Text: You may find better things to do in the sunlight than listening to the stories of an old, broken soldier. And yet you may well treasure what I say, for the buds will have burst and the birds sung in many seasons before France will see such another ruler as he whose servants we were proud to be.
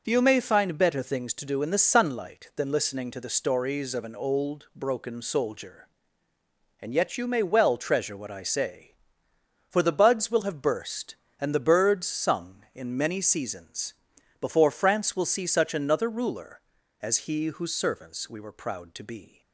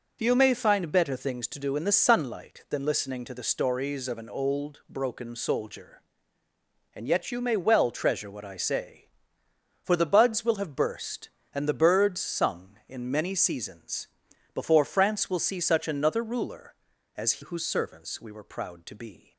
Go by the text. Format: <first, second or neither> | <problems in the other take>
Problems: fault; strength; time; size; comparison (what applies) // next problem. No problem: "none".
first | pauses between "seasons" and "before"; noticeable; at 14.0 s; 0.46 s long; noticeable in the first // skips "he"; at 17.4 s